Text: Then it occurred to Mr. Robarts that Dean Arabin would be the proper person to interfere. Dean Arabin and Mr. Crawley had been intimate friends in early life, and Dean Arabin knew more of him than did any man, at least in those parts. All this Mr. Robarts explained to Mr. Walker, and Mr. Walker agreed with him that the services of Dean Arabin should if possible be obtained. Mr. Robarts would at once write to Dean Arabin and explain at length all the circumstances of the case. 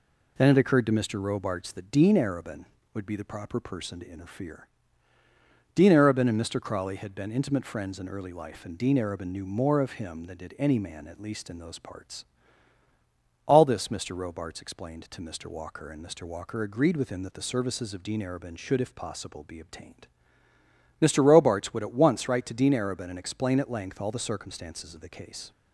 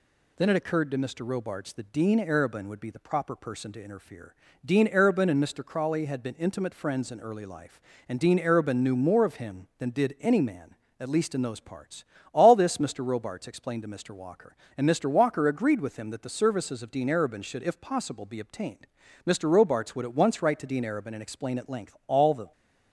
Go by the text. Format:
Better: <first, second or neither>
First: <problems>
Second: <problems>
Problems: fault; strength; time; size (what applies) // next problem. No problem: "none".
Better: first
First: none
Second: stops before "circumstances of the case"; at 22.5 s